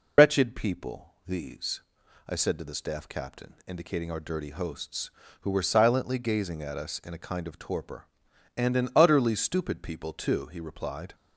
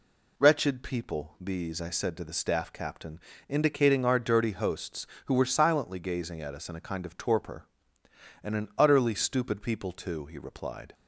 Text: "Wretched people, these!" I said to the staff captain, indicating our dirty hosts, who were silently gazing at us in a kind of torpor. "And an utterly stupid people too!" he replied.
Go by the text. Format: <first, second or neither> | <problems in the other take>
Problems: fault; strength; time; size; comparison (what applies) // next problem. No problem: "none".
second | loses the start of "Wretched"; at 0.1 s; 120 ms